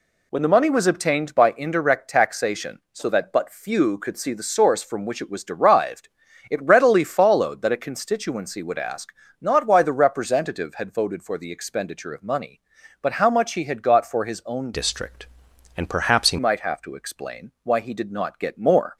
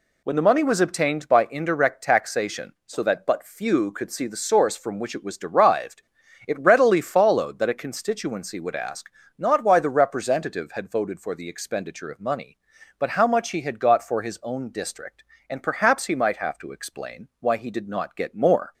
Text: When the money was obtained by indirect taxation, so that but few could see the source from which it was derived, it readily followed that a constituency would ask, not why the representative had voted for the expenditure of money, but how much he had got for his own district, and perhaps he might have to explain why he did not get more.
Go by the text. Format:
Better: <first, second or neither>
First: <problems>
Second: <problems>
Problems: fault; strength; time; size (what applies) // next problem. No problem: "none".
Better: second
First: changes voice from "district" to "he"; from 14.7 to 16.3 s; 1.6 s long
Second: none